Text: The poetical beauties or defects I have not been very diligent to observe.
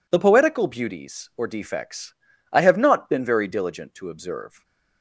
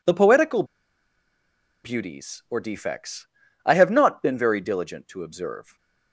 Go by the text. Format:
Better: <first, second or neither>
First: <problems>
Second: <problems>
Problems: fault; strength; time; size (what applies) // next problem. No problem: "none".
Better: first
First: pauses between "defects" and "I"; at 2.1 s; 0.38 s long // stays silent after the last word; slight; from 4.4 s on; 0.6 s long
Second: pauses between "poetical" and "beauties"; at 0.6 s; 1.2 s long // pauses between "defects" and "I"; at 3.2 s; 0.38 s long // stays silent after the last word; slight; from 5.6 s on; 0.5 s long